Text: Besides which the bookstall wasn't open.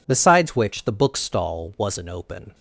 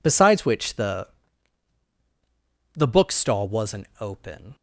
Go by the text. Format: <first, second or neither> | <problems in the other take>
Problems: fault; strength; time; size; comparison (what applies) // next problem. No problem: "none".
first | says "the" twice; at 2.7 s